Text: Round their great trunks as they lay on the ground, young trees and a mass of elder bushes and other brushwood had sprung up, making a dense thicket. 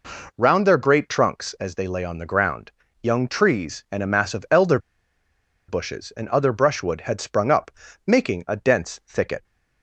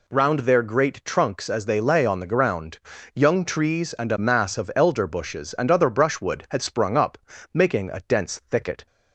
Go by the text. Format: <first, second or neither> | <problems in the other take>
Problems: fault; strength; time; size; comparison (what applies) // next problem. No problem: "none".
second | pauses between "elder" and "bushes"; noticeable; at 4.7 s; 0.90 s long